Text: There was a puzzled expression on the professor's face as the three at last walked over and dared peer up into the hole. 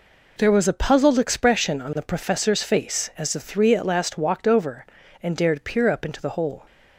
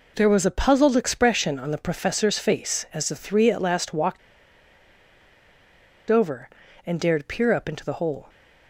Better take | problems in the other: first | pauses between "walked" and "over"; strong; at 4.1 s; 1.9 s long

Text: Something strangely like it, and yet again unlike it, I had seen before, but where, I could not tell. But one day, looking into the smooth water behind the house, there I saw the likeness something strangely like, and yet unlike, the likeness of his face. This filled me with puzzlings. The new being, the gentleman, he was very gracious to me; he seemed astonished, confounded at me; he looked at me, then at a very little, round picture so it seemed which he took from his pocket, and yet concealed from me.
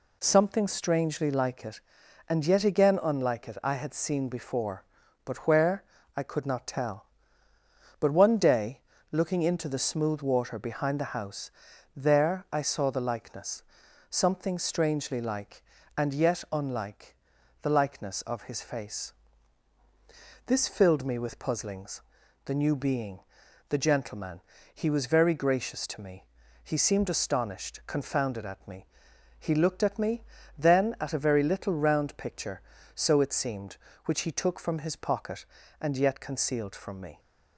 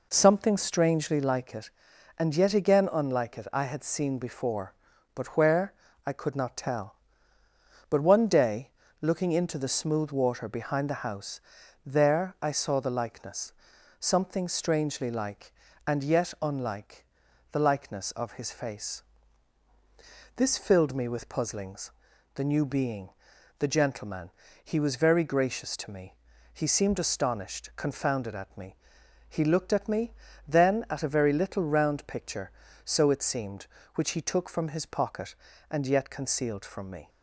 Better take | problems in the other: first | starts louder than the rest; noticeable; until 1.2 s; 4 dB // pauses between "likeness" and "something"; noticeable; at 13.5 s; 0.48 s long; noticeable in the first

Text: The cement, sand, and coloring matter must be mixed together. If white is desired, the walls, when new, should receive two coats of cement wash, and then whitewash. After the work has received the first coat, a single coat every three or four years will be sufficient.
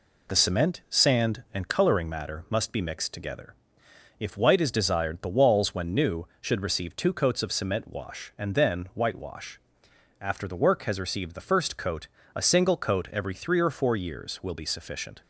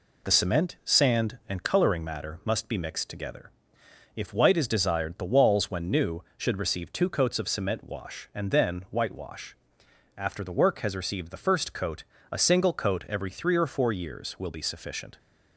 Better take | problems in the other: neither | none

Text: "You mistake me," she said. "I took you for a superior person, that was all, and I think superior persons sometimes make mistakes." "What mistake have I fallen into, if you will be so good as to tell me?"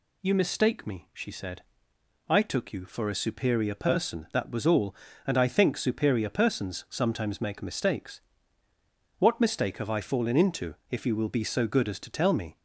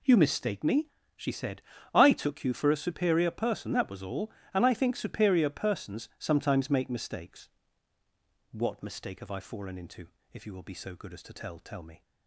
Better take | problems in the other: first | says "tell" twice; at 11.5 s

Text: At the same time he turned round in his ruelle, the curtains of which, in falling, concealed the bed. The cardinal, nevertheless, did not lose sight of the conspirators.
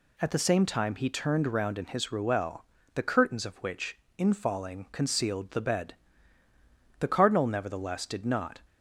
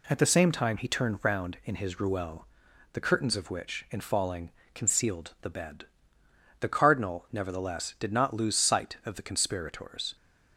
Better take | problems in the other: second | stops before "lose sight of the conspirators"; at 8.6 s

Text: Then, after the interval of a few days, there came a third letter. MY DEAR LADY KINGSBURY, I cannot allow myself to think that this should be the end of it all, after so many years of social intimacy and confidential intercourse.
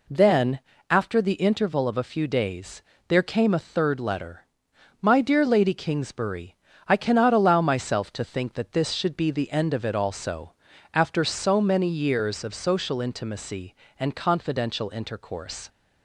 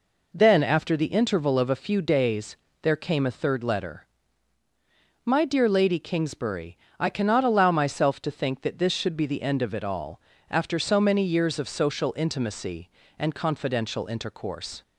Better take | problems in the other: second | says "also" for "all"; at 9.9 s

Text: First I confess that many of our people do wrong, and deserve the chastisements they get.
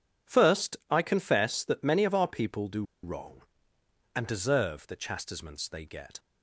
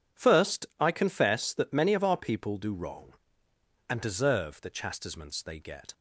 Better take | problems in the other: second | pauses between "do" and "wrong"; slight; at 2.8 s; 0.20 s long

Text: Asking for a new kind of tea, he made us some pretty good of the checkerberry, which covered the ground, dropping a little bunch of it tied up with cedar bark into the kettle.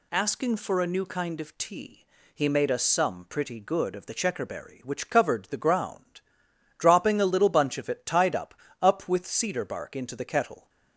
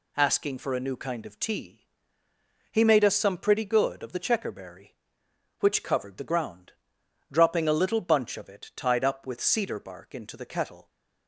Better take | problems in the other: second | says "up" twice; at 8.8 s

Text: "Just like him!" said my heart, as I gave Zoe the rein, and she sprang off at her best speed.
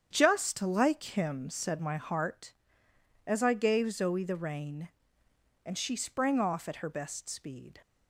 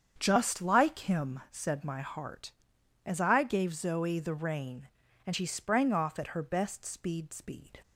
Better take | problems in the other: first | starts louder than the rest; strong; until 1.1 s; 7.5 dB; strong in the first // says "speed" twice; at 7.3 s

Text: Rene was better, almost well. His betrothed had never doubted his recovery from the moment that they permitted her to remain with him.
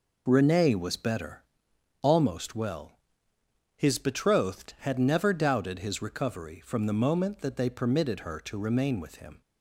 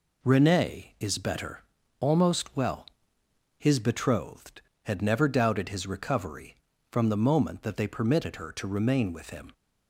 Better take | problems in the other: first | says "is" for "was"; at 1.0 s

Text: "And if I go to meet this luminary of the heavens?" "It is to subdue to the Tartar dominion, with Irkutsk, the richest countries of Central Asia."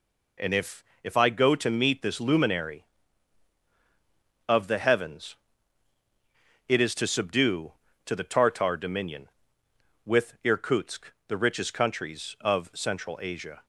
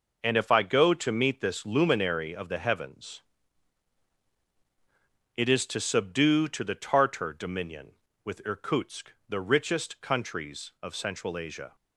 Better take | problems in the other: second | says "if" twice; at 1.0 s

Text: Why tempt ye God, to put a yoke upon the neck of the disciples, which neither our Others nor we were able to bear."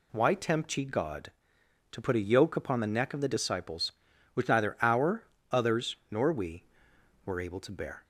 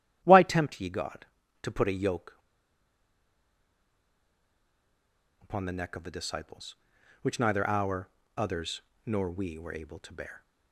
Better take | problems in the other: first | starts louder than the rest; strong; until 1.2 s; 10.5 dB // pauses between "yoke" and "upon"; strong; at 2.3 s; 3.0 s long // pauses between "our" and "Others"; slight; at 8.0 s; 0.30 s long; slight in the first // pauses between "Others" and "nor"; slight; at 8.7 s; 0.24 s long; slight in the first

